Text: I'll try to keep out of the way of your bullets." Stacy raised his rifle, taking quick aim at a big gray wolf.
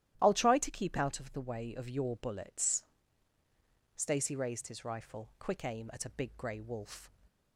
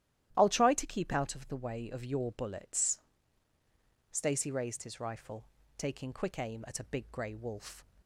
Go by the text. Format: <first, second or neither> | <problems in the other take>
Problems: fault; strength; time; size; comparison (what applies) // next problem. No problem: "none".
second | starts louder than the rest; strong; until 1.2 s; 12.5 dB; strong in the second // skips "taking"; at 5.3 s